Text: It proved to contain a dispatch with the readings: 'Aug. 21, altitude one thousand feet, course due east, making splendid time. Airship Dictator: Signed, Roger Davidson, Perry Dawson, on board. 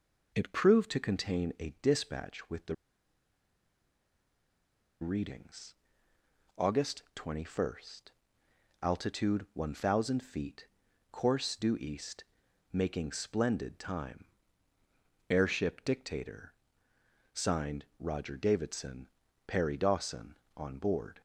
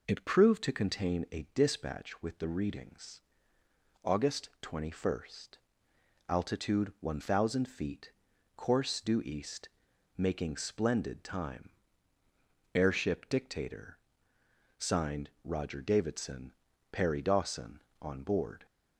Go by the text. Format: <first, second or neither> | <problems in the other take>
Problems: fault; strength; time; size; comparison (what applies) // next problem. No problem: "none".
second | pauses between "the" and "readings"; strong; at 2.7 s; 2.2 s long